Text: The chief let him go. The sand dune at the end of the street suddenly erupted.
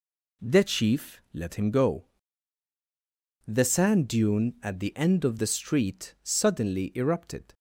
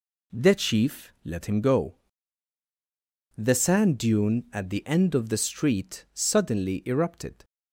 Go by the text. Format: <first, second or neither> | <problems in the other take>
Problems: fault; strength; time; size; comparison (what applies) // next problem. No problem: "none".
neither | none